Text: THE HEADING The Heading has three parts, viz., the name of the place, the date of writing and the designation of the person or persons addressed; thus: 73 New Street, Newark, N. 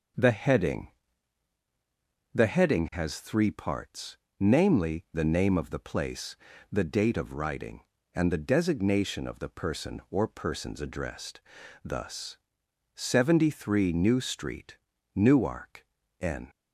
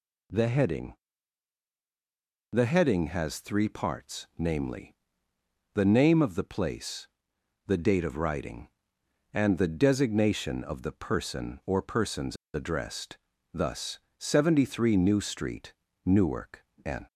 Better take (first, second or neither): first